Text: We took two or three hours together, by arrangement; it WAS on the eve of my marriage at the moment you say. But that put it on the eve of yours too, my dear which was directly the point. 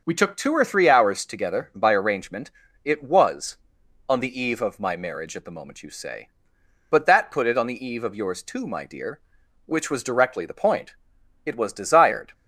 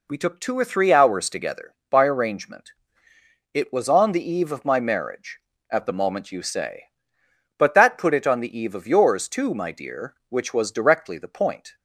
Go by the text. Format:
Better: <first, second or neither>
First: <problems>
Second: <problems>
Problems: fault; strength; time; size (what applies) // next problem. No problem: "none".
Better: second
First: starts louder than the rest; until 1.0 s; 6.5 dB // goes on to say "It was desired"; noticeable; from 11.4 s on; 0.88 s long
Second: none